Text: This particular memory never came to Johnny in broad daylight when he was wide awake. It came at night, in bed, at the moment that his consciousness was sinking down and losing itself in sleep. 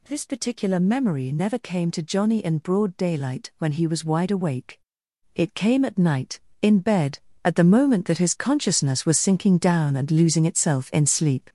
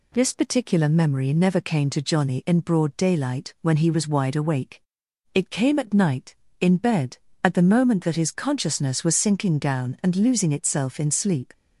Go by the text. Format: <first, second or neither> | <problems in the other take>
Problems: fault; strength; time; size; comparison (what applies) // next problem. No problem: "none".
second | gets louder; throughout; 7 dB